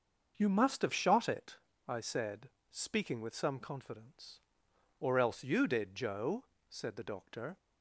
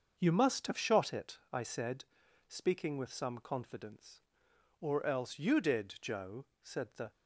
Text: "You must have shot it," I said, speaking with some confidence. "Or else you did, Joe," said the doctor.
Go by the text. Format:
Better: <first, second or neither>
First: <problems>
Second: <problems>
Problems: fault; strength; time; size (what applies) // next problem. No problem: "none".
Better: first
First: starts louder than the rest; until 1.3 s; 6.5 dB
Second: starts louder than the rest; until 1.2 s; 6.5 dB // stops before "doctor"; at 7.1 s